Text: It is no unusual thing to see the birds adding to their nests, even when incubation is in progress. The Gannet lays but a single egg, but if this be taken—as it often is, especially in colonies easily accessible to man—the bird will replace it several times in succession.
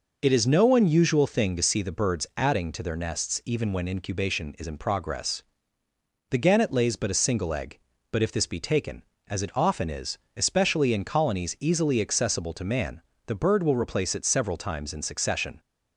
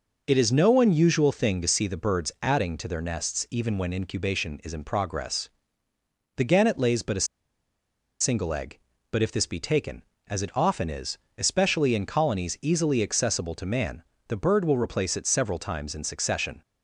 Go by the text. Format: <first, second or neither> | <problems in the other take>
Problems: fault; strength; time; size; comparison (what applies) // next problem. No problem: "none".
first | pauses between "a" and "single"; noticeable; at 7.2 s; 0.94 s long